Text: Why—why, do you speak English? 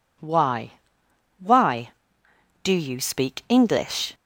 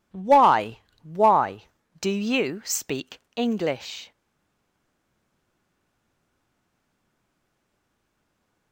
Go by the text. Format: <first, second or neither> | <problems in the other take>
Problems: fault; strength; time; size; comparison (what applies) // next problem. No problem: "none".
first | pauses between "speak" and "English"; slight; at 3.1 s; 0.18 s long // stays silent after the last word; strong; from 4.1 s on; 4.6 s long